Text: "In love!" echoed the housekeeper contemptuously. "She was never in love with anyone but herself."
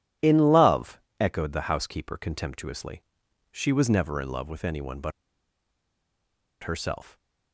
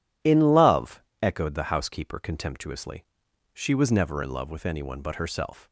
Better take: second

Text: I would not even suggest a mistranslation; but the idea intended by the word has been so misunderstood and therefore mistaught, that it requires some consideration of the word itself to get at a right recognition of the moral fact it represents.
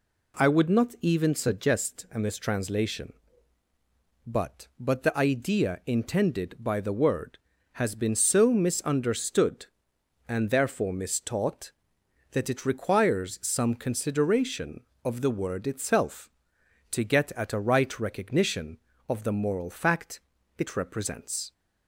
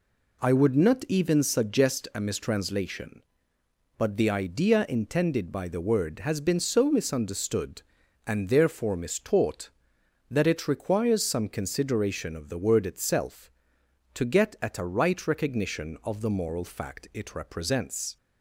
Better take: second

